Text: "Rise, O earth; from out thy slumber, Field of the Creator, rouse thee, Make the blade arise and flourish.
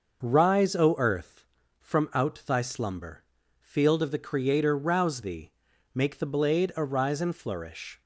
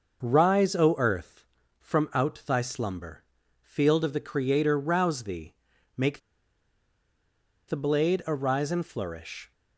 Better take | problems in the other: first | pauses between "Make" and "the"; strong; at 6.2 s; 1.4 s long

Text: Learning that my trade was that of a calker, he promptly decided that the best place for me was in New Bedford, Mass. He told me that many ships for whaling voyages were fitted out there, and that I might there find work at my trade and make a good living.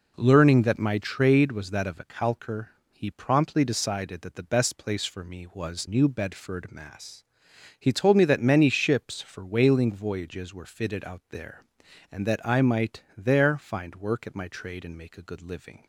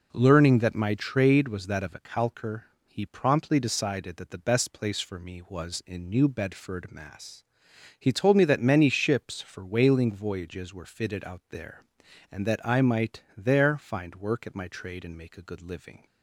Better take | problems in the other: second | skips "in"; at 5.8 s // pauses between "might" and "there"; slight; at 13.0 s; 0.16 s long; slight in the second

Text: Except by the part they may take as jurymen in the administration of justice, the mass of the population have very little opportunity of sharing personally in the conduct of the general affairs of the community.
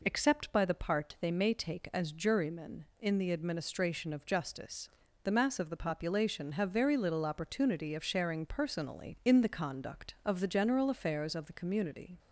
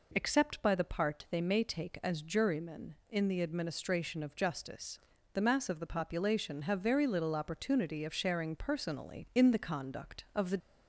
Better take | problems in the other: first | stops before "general affairs of the community"; at 10.6 s

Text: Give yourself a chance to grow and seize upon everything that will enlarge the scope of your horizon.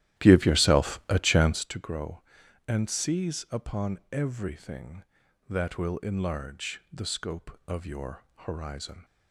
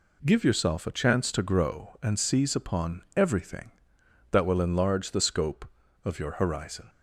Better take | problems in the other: second | starts louder than the rest; strong; until 1.7 s; 14 dB

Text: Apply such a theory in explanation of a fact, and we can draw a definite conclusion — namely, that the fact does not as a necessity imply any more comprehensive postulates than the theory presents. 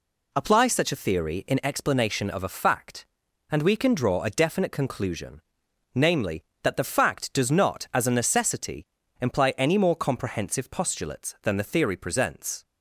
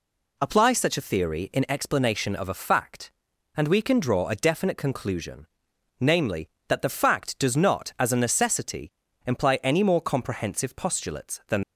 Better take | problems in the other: first | pauses between "necessity" and "imply"; slight; at 8.9 s; 0.34 s long; slight in the first // stops before "the theory presents"; at 11.6 s

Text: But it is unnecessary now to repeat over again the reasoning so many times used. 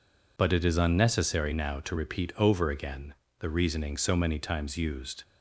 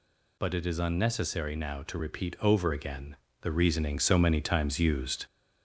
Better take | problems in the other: first | gets louder; slight; throughout; 2 dB // pauses between "again" and "the"; slight; at 3.1 s; 0.26 s long; slight in the first

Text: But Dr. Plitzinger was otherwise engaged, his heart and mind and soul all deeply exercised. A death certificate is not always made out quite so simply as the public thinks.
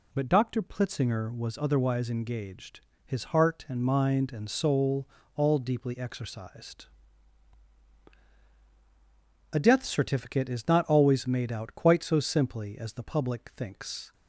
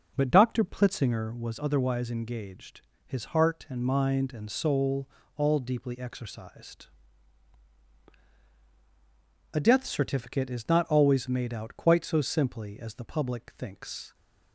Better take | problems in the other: first | starts louder than the rest; noticeable; until 1.1 s; 5.5 dB // pauses between "soul" and "all"; slight; at 5.0 s; 0.28 s long; slight in the first

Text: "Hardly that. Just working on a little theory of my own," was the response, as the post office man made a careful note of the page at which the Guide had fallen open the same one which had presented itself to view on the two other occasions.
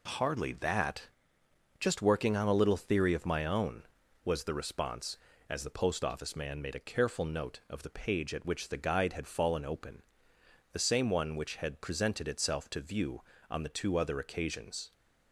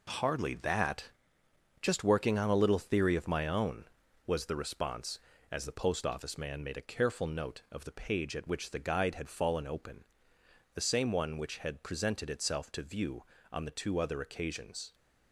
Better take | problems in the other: first | gets quieter; strong; throughout; 8 dB // pauses between "open" and "the"; noticeable; at 10.0 s; 0.68 s long; noticeable in the first

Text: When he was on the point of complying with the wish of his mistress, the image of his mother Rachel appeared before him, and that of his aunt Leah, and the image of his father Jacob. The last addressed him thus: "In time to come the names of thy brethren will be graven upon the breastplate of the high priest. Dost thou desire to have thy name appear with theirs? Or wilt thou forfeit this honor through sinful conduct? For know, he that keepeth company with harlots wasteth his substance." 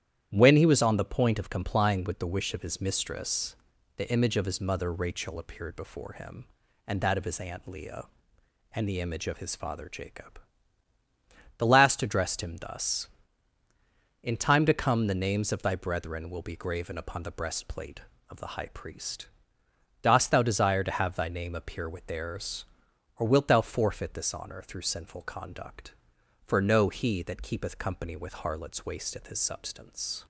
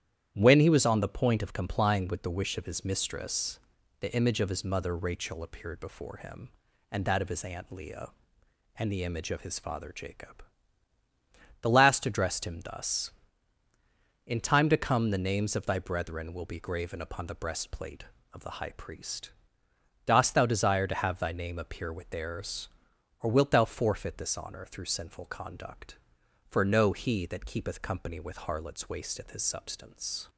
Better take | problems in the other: neither | starts louder than the rest; strong; the same in both

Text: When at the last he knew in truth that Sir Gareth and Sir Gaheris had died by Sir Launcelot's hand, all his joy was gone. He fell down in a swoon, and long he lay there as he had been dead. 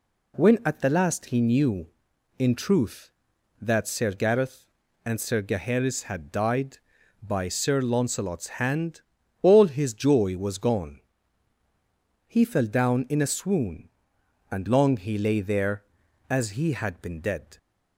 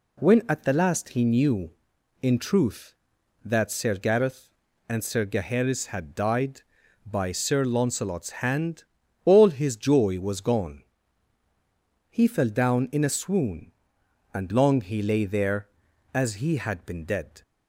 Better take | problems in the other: neither | none

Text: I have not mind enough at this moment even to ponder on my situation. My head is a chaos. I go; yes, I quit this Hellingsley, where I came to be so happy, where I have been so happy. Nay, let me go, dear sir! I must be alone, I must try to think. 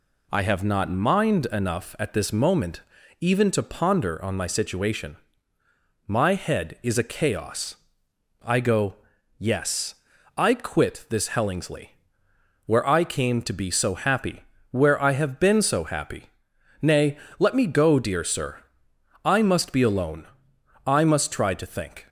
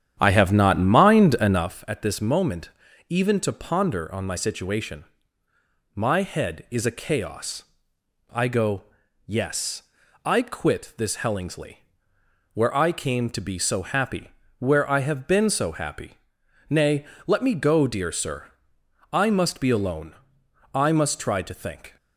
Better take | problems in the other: first | starts louder than the rest; strong; until 1.8 s; 9.5 dB // pauses between "moment" and "even"; at 2.7 s; 0.38 s long; also in the first

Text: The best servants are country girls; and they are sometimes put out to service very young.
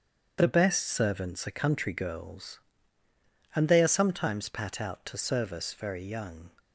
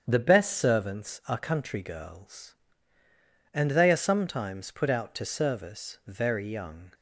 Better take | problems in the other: second | starts louder than the rest; strong; until 1.4 s; 8 dB; strong in the second // says "pat" for "put"; at 4.4 s

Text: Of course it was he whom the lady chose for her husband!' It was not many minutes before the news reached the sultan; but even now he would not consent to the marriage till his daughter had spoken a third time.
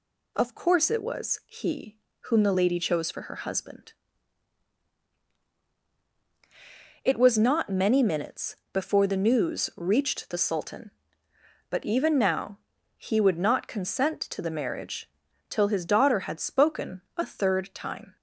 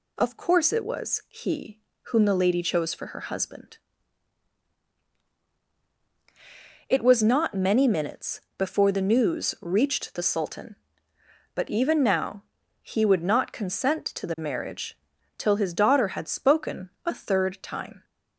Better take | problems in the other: neither | pauses between "he" and "whom"; slight; the same in both // pauses between "minutes" and "before"; slight; the same in both // pauses between "now" and "he"; the same in both // pauses between "marriage" and "till"; the same in both // pauses between "spoken" and "a"; slight; the same in both

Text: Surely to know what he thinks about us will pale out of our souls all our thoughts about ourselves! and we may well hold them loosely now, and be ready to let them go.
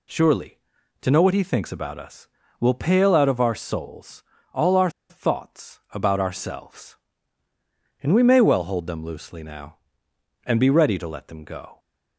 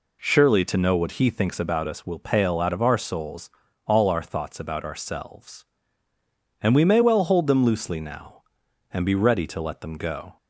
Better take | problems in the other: second | pauses between "souls" and "all"; slight; at 4.2 s; 0.32 s long; slight in the second // pauses between "our" and "thoughts"; slight; at 4.8 s; 0.20 s long

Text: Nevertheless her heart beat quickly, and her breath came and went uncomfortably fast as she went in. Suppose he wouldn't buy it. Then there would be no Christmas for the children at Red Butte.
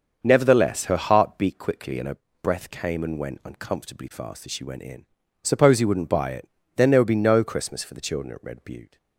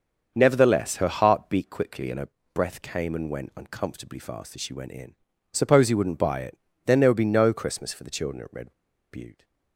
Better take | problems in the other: first | starts louder than the rest; until 1.3 s; 6.5 dB; also in the first // pauses between "her" and "breath"; slight; at 2.2 s; 0.24 s long; slight in the first // pauses between "Red" and "Butte"; at 8.7 s; 0.37 s long

